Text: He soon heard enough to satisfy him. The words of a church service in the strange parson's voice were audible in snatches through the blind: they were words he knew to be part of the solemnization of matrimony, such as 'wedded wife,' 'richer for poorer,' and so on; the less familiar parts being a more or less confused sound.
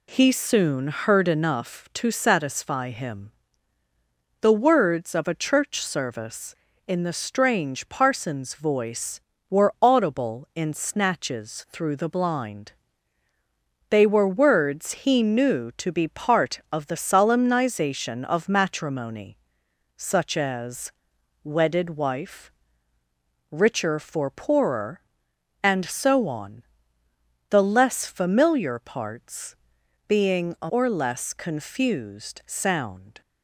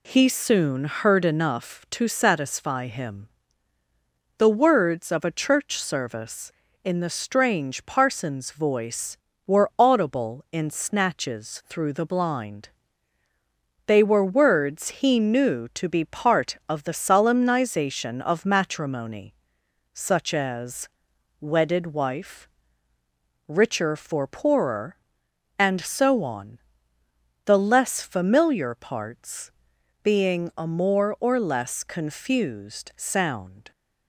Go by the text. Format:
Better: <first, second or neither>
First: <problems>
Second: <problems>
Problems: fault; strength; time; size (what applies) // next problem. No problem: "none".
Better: second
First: pauses between "as" and "wedded"; noticeable; at 20.9 s; 0.52 s long // pauses between "parts" and "being"; noticeable; at 29.5 s; 0.52 s long // skips "more"; at 30.6 s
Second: pauses between "as" and "wedded"; noticeable; at 20.8 s; 0.52 s long // pauses between "parts" and "being"; noticeable; at 29.5 s; 0.52 s long